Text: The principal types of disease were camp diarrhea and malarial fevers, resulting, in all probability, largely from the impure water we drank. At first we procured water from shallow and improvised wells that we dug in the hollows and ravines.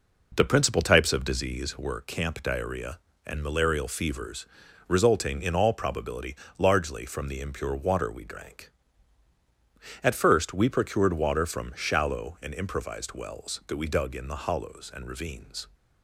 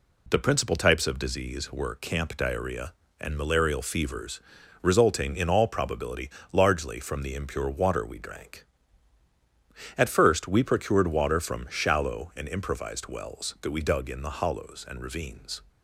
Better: second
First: starts louder than the rest; noticeable; until 1.8 s; 4.5 dB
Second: none

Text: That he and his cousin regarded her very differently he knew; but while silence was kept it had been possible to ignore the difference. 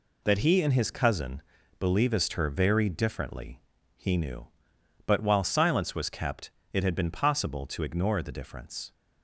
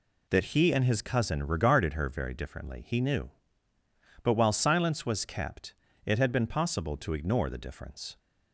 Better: second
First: says "believest" for "regarded"; at 1.7 s // pauses between "differently" and "he"; slight; at 3.6 s; 0.36 s long // pauses between "kept" and "it"; slight; at 6.5 s; 0.22 s long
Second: pauses between "kept" and "it"; slight; at 5.7 s; 0.28 s long

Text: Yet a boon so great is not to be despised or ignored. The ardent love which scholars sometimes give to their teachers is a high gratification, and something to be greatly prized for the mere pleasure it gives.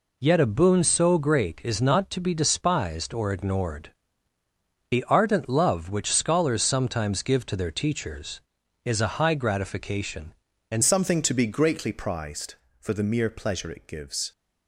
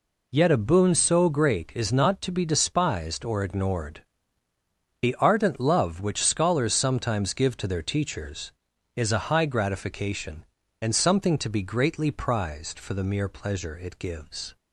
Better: second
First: changes voice at "something"; from 10.8 s on; 3.5 s long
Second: none

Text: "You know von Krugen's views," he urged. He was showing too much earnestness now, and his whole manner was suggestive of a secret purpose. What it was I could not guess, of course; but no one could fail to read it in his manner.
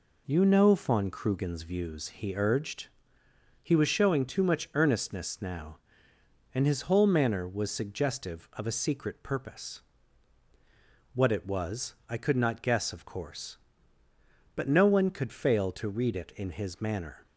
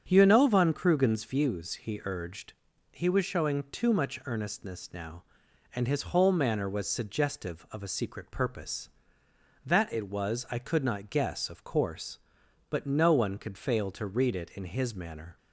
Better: first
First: none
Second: starts louder than the rest; strong; until 1.0 s; 7.5 dB // says "That" for "What"; at 9.6 s

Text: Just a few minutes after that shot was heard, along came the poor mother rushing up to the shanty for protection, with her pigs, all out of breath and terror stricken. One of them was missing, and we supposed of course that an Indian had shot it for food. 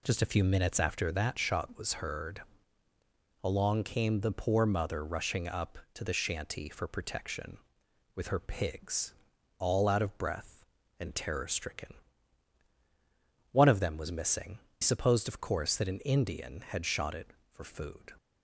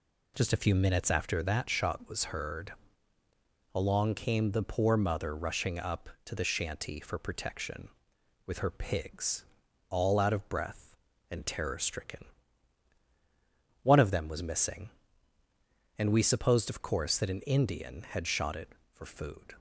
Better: second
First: skips "and we"; at 14.6 s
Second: none

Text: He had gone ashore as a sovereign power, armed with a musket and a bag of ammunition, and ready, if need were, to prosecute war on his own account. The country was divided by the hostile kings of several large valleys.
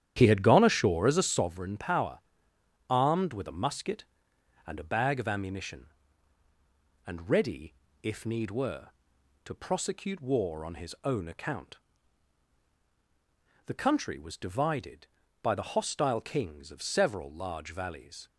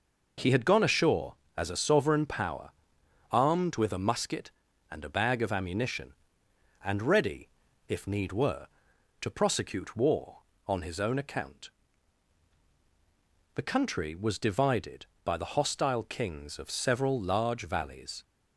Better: second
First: starts louder than the rest; strong; until 1.4 s; 10.5 dB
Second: none

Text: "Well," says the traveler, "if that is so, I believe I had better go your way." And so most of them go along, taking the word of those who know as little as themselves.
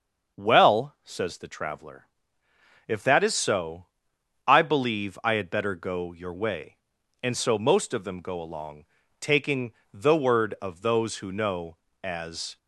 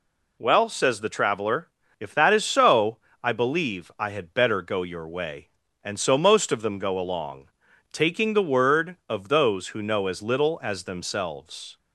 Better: second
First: starts louder than the rest; until 1.4 s; 6.5 dB // pauses between "taking" and "the"; slight; at 9.7 s; 0.22 s long // stops before "little as themselves"; at 12.5 s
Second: none

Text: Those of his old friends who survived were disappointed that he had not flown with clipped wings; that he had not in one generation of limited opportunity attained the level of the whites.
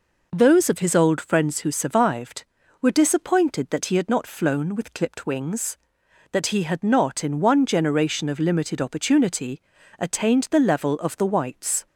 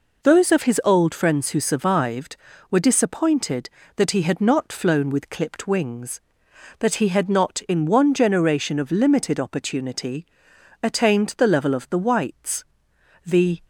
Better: first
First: pauses between "opportunity" and "attained"; at 9.5 s; 0.38 s long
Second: pauses between "opportunity" and "attained"; noticeable; at 10.2 s; 0.56 s long // goes on to say "The"; slight; from 13.2 s on; 0.36 s long

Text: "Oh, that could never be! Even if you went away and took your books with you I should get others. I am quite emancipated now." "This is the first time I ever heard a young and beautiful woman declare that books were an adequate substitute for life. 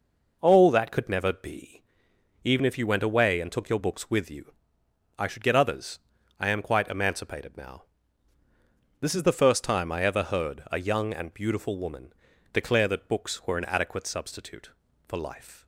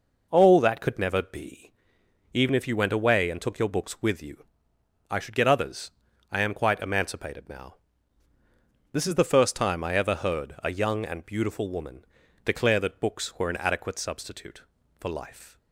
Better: neither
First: pauses between "you" and "I"; noticeable; at 4.5 s; 0.66 s long // pauses between "woman" and "declare"; at 12.1 s; 0.40 s long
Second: pauses between "you" and "I"; noticeable; at 4.4 s; 0.66 s long // pauses between "woman" and "declare"; at 12.0 s; 0.40 s long

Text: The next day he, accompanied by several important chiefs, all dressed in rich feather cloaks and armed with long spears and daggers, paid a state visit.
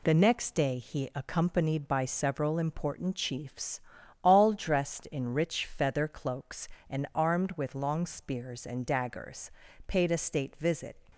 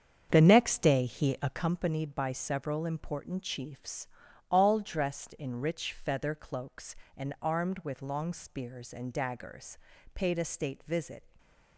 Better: first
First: none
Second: starts louder than the rest; strong; until 1.7 s; 7.5 dB // stays silent after the last word; slight; from 11.2 s on; 0.5 s long

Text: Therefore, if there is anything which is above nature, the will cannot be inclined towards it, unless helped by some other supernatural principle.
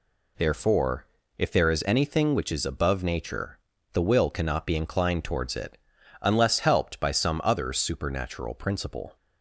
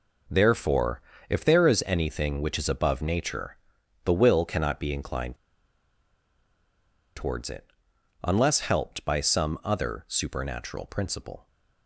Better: first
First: none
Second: pauses between "inclined" and "towards"; strong; at 5.3 s; 1.8 s long

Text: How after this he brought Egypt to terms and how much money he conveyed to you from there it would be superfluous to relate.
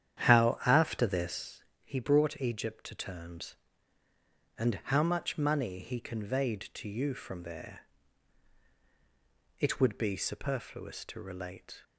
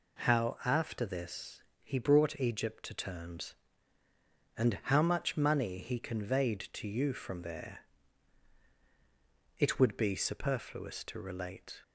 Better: second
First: starts louder than the rest; strong; until 1.5 s; 9.5 dB // pauses between "this" and "he"; slight; at 1.6 s; 0.22 s long // pauses between "there" and "it"; strong; at 7.8 s; 1.8 s long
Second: pauses between "this" and "he"; slight; at 1.6 s; 0.22 s long // pauses between "there" and "it"; strong; at 7.7 s; 1.8 s long

